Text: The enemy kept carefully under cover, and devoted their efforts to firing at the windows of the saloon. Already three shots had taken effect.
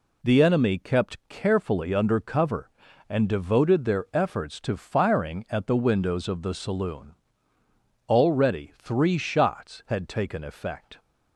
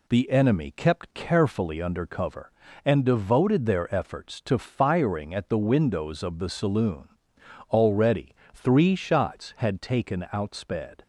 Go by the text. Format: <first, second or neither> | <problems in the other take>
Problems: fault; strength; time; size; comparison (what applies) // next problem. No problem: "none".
first | pauses between "Already" and "three"; slight; at 8.3 s; 0.20 s long // says "outsped" for "effect"; at 10.3 s